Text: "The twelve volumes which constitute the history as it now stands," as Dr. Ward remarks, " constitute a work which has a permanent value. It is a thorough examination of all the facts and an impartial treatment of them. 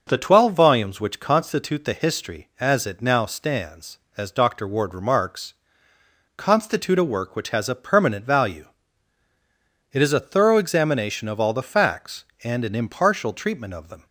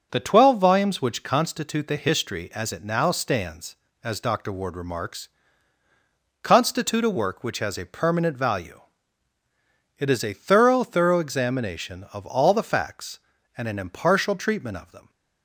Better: first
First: starts louder than the rest; until 1.0 s; 6 dB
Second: starts louder than the rest; strong; until 1.1 s; 7 dB // says "thorough" twice; at 10.8 s

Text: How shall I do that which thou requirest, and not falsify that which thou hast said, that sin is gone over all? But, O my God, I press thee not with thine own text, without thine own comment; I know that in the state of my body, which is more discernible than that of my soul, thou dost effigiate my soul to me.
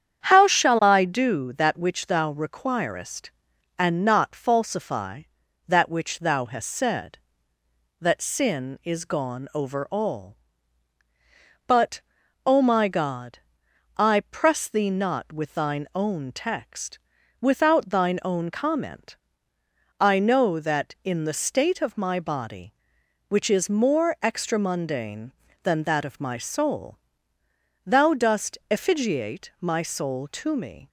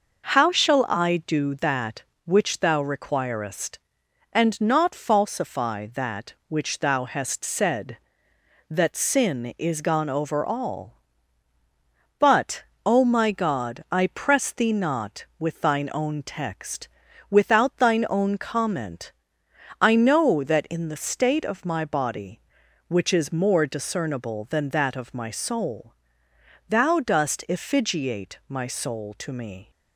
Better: second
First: starts louder than the rest; strong; until 1.2 s; 8.5 dB // says "extramundane" for "discernible"; at 24.2 s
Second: none

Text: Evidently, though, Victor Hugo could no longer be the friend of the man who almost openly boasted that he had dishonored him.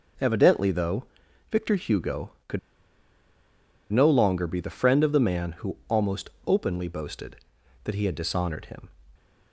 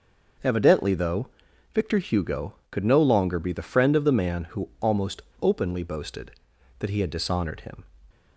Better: second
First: starts louder than the rest; until 1.6 s; 6.5 dB // pauses between "could" and "no"; strong; at 2.5 s; 1.3 s long // pauses between "almost" and "openly"; slight; at 6.2 s; 0.16 s long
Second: starts louder than the rest; noticeable; until 1.8 s; 6 dB // pauses between "almost" and "openly"; slight; at 5.2 s; 0.18 s long

